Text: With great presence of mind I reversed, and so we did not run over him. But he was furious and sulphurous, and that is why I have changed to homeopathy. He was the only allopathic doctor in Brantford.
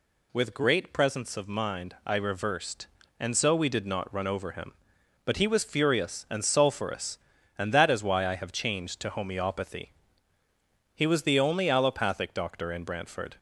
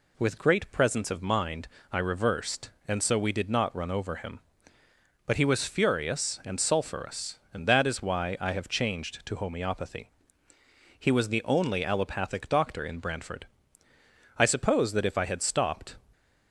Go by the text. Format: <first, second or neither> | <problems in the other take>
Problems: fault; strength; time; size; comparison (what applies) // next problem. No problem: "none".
first | pauses between "mind" and "I"; slight; at 1.6 s; 0.24 s long // goes on to say "I suppose that if I had stopped"; from 14.3 s on; 1.6 s long